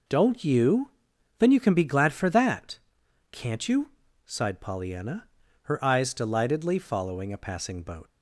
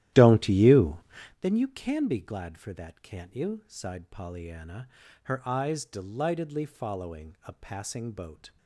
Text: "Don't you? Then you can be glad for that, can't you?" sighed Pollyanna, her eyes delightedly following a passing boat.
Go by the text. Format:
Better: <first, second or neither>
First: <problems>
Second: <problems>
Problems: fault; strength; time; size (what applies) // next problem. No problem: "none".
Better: first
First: none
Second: starts louder than the rest; strong; until 1.4 s; 13.5 dB